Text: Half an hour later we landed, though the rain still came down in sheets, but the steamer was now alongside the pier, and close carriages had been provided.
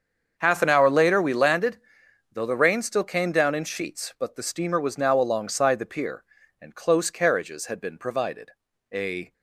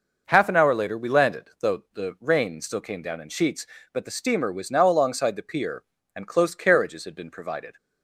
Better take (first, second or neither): second